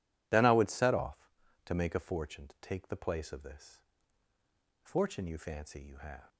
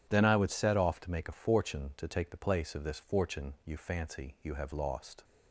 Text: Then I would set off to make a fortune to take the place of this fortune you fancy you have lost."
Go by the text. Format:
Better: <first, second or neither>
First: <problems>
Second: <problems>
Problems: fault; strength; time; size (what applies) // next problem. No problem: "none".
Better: second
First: pauses between "this" and "fortune"; at 3.8 s; 1.0 s long // stops before "lost"; at 6.2 s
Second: none